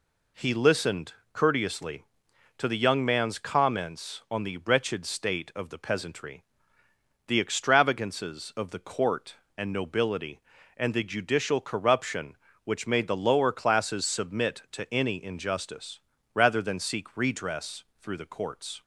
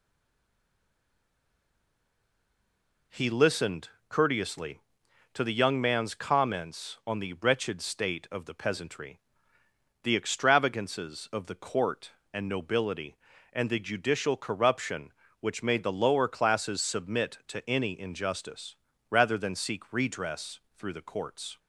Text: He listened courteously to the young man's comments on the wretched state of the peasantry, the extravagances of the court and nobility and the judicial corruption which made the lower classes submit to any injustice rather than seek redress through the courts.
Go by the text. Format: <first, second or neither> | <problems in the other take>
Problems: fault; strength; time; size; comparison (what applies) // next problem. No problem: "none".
first | stays silent before the first word; strong; until 3.1 s; 3.1 s long // pauses between "listened" and "courteously"; slight; at 3.8 s; 0.20 s long; slight in the first // pauses between "injustice" and "rather"; slight; at 18.7 s; 0.34 s long; slight in the first // pauses between "redress" and "through"; slight; at 20.6 s; 0.16 s long; slight in the first